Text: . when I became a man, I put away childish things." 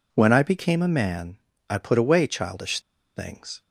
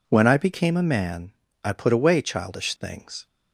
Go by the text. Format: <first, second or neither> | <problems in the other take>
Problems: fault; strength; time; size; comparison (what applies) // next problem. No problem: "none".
second | pauses between "childish" and "things"; slight; at 2.8 s; 0.34 s long